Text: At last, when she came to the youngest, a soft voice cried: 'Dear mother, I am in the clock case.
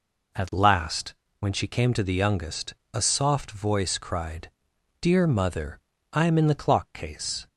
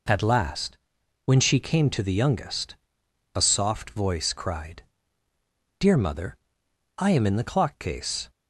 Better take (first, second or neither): neither